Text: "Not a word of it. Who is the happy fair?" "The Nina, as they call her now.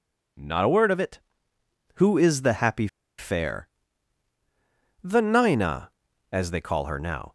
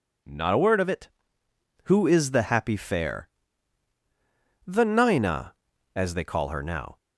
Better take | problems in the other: second | pauses between "happy" and "fair"; slight; at 2.8 s; 0.30 s long

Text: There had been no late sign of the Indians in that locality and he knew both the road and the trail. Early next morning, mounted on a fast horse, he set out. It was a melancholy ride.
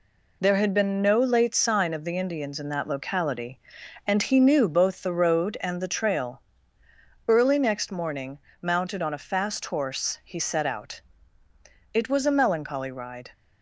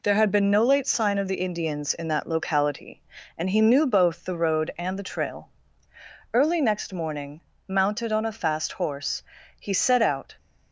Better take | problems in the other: first | stops before "It was a melancholy ride"; at 10.3 s

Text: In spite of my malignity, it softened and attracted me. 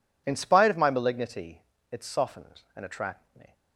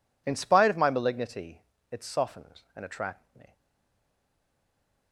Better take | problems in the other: first | stays silent after the last word; noticeable; from 3.5 s on; 1.6 s long

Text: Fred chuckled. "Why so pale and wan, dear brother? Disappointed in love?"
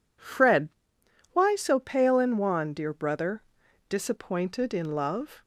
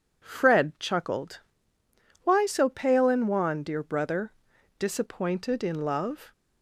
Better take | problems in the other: second | skips "chuckled"; at 1.0 s

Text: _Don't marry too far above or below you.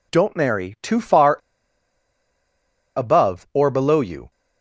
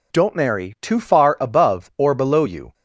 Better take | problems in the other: second | pauses between "far" and "above"; strong; at 1.3 s; 1.5 s long

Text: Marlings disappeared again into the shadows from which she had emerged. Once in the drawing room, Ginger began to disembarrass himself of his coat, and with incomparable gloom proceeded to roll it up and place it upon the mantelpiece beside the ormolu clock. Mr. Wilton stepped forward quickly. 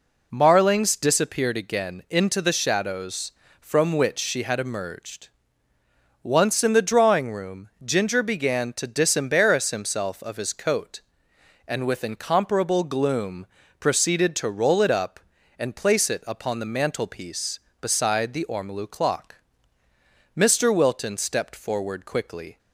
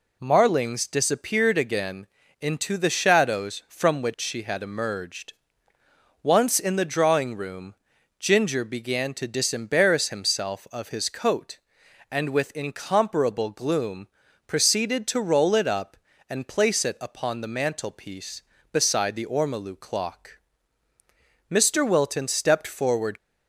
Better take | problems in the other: first | pauses between "again" and "into"; slight; at 2.0 s; 0.34 s long // pauses between "gloom" and "proceeded"; at 14.0 s; 0.40 s long; slight in the first // stops before "quickly"; at 23.1 s

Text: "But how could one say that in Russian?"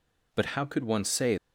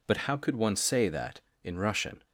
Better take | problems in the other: second | stops before "that in Russian"; at 1.3 s

